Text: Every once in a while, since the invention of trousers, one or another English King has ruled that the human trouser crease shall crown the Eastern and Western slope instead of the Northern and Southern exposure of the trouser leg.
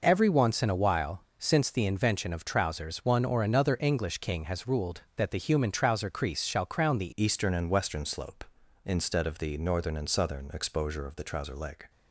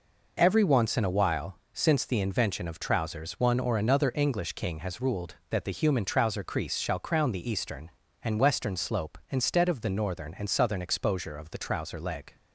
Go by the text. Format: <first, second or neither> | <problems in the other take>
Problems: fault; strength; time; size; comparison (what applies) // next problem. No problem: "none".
second | changes voice at "Eastern"; from 7.1 s on; 4.7 s long